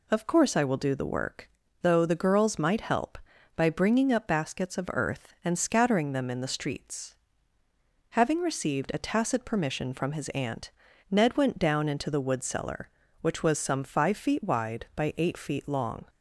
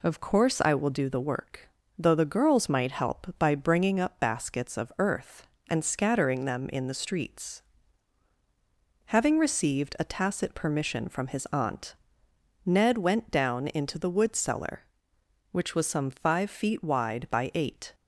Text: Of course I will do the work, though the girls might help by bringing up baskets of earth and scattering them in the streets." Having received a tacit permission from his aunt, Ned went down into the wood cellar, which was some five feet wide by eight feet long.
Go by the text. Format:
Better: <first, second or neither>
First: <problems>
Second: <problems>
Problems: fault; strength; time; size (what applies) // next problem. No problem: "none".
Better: first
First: none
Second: stops before "feet long"; at 17.9 s